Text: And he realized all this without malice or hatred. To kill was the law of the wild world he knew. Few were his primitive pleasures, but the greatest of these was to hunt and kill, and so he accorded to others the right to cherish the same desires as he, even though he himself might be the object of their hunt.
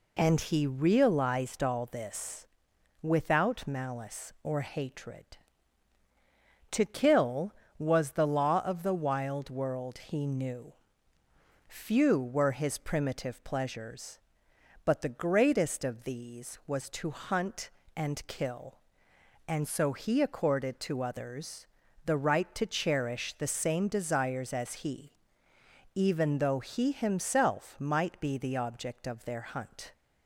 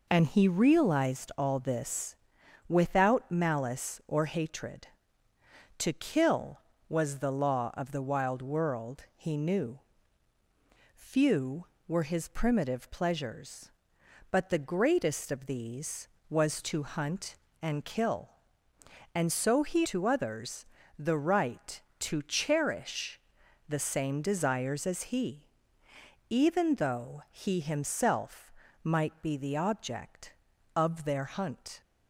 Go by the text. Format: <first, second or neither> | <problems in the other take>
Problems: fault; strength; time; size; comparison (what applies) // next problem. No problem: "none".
first | pauses between "this" and "without"; noticeable; at 2.1 s; 0.52 s long; noticeable in the first // skips "accorded"; at 19.8 s // pauses between "others" and "the"; slight; at 20.6 s; 0.34 s long; also in the first // pauses between "cherish" and "the"; noticeable; at 23.1 s; 0.50 s long // pauses between "himself" and "might"; slight; at 28.5 s; 0.32 s long